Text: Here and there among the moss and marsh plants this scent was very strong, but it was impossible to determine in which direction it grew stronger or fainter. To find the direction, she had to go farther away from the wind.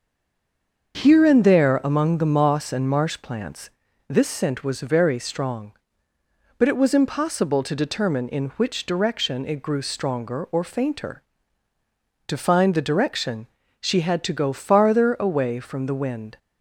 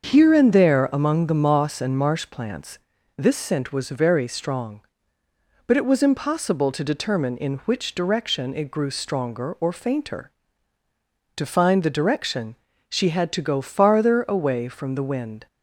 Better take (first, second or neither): second